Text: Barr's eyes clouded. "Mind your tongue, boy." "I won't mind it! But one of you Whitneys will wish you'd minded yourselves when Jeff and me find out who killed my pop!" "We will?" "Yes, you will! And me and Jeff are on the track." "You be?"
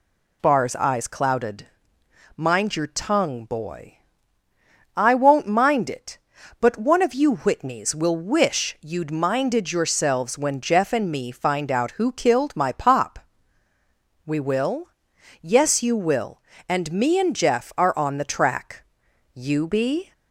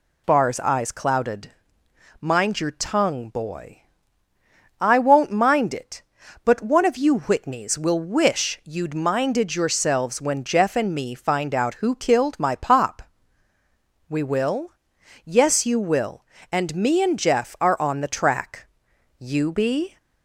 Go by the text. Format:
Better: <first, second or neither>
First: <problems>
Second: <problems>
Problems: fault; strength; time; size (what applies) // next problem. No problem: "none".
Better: neither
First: none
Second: none